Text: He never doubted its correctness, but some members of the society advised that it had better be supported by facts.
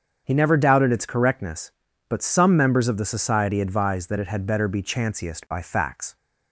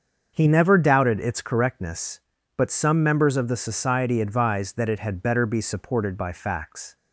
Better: second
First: starts louder than the rest; strong; until 1.2 s; 7 dB // says "chanciest" for "supported"; at 4.8 s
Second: starts louder than the rest; until 1.3 s; 7 dB

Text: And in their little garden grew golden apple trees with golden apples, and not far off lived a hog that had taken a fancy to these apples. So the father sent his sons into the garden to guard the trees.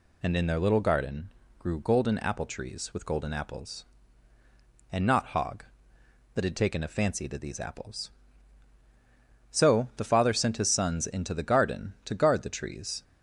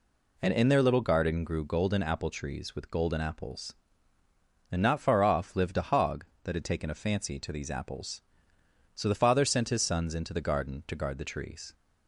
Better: second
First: pauses between "garden" and "grew"; slight; at 1.2 s; 0.30 s long // skips "far off lived a"; at 5.2 s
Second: none

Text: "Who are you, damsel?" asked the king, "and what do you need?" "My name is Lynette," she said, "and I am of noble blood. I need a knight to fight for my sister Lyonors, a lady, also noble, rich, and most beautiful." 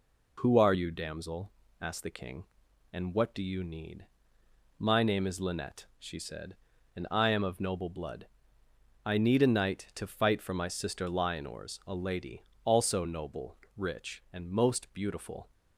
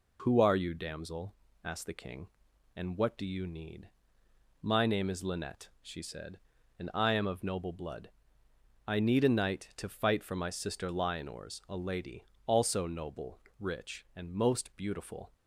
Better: neither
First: none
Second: none

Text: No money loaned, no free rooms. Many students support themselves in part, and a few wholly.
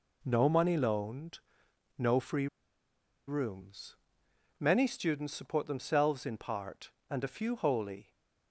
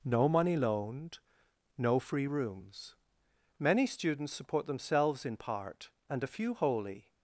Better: second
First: pauses between "free" and "rooms"; noticeable; at 2.4 s; 0.81 s long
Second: none

